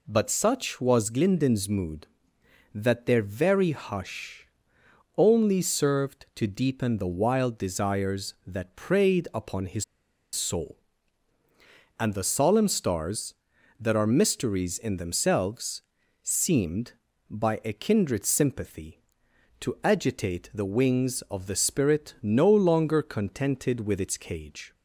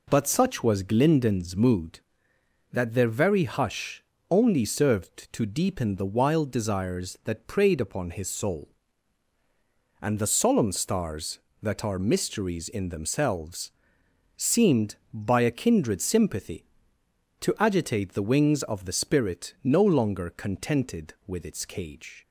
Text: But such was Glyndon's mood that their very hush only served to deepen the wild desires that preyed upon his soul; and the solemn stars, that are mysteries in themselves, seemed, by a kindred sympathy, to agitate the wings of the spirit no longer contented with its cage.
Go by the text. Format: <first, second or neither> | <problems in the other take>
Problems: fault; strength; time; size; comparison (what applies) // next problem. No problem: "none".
second | pauses between "hush" and "only"; noticeable; at 4.4 s; 0.70 s long; slight in the second // pauses between "his" and "soul"; noticeable; at 9.8 s; 0.49 s long